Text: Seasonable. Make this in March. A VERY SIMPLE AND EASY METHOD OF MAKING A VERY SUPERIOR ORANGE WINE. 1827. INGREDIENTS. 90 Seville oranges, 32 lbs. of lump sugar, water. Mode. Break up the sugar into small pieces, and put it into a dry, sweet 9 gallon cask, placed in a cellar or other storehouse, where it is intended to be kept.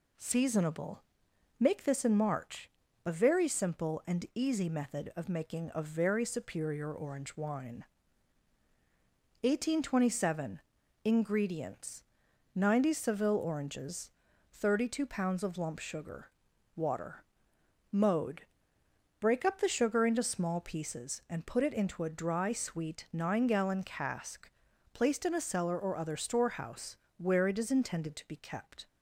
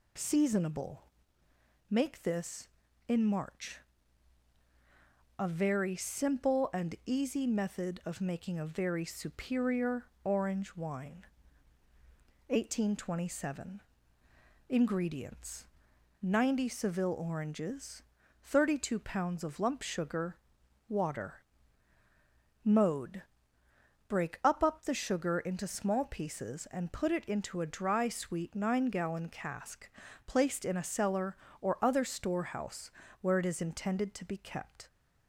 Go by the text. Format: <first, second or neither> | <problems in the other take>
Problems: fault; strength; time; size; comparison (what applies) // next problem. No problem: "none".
first | pauses between "SUPERIOR" and "ORANGE"; slight; at 10.0 s; 0.18 s long // says "up" twice; at 24.6 s